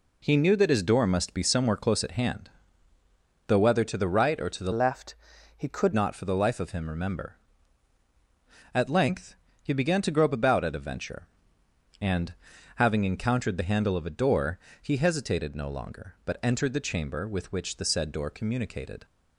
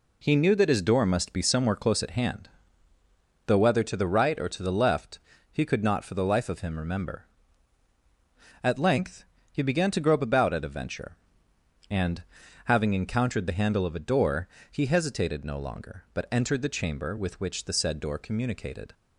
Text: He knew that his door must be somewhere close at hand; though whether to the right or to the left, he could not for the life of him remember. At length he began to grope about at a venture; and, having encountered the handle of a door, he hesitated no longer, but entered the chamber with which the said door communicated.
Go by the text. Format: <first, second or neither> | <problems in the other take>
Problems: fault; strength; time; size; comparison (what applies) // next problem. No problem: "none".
second | changes voice from "left" to "could"; from 4.7 to 5.9 s; 1.2 s long // pauses between "length" and "he"; slight; at 9.3 s; 0.26 s long; slight in the second